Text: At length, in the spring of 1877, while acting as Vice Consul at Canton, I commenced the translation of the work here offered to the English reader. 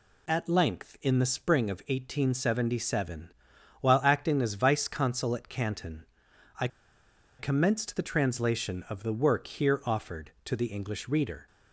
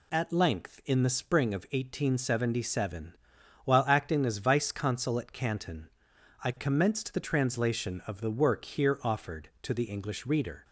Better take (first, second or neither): second